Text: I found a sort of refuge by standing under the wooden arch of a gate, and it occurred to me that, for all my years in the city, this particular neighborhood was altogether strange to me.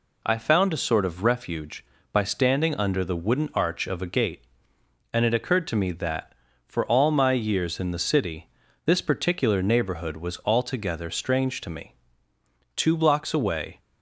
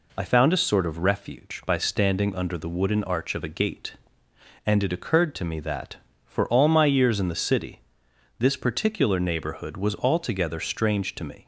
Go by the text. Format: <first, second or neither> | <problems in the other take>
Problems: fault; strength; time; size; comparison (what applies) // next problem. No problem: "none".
second | goes on to say "Two blocks away"; noticeable; from 12.7 s on; 1.0 s long